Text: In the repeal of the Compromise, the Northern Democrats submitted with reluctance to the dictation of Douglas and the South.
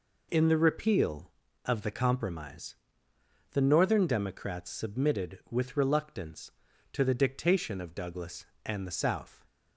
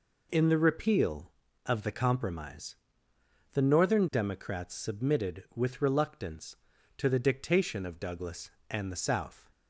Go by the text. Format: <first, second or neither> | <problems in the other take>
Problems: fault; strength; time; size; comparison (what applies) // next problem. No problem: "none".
neither | none